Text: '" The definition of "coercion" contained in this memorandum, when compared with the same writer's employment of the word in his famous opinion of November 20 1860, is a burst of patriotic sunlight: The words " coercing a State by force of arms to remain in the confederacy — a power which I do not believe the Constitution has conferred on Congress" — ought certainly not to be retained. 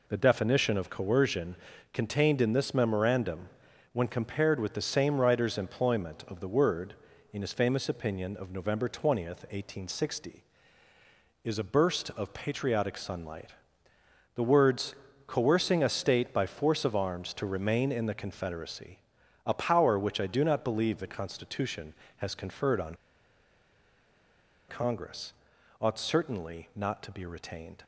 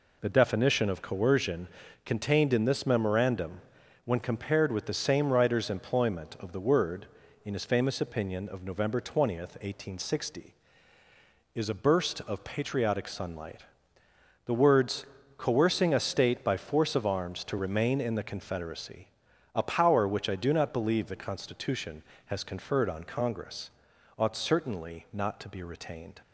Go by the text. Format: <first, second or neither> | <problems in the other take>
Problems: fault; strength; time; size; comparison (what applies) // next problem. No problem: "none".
second | pauses between "coercion" and "contained"; at 1.5 s; 0.38 s long; also in the second // pauses between "on" and "Congress"; strong; at 22.9 s; 1.7 s long